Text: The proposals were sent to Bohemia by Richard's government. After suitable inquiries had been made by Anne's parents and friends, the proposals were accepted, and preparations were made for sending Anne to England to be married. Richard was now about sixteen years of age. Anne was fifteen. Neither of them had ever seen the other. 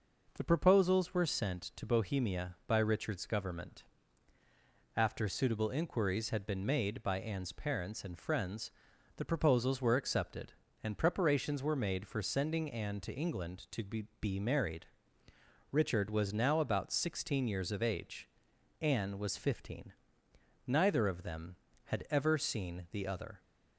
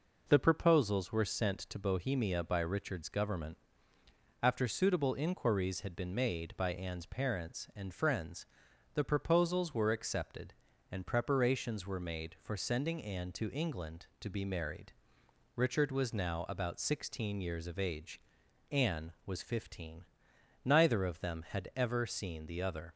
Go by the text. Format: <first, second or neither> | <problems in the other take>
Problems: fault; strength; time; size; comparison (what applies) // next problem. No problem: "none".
second | says "be" twice; at 14.2 s